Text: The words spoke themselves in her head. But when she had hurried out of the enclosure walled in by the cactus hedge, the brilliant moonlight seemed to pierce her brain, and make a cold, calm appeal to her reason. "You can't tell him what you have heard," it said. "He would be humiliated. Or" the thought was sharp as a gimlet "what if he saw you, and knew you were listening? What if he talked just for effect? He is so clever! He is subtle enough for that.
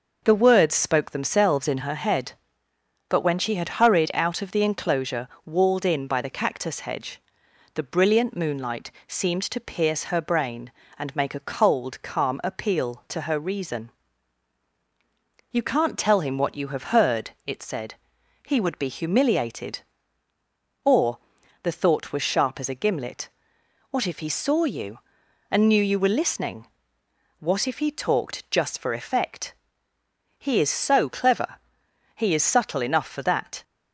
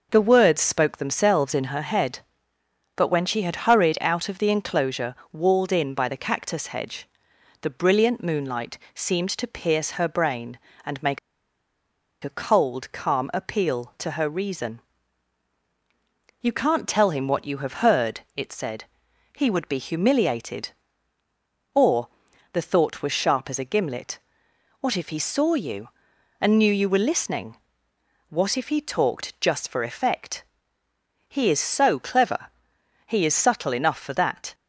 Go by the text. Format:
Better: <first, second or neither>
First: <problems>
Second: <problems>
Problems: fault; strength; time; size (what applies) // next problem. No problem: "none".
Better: first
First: pauses between "enclosure" and "walled"; slight; at 5.2 s; 0.18 s long // pauses between "moonlight" and "seemed"; slight; at 8.9 s; 0.16 s long // pauses between "Or" and "the"; at 21.1 s; 0.44 s long // pauses between "gimlet" and "what"; noticeable; at 23.2 s; 0.62 s long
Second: pauses between "enclosure" and "walled"; slight; at 5.1 s; 0.18 s long // pauses between "moonlight" and "seemed"; slight; at 8.7 s; 0.16 s long // pauses between "make" and "a"; at 11.1 s; 1.0 s long // pauses between "Or" and "the"; at 22.0 s; 0.44 s long // pauses between "gimlet" and "what"; noticeable; at 24.1 s; 0.62 s long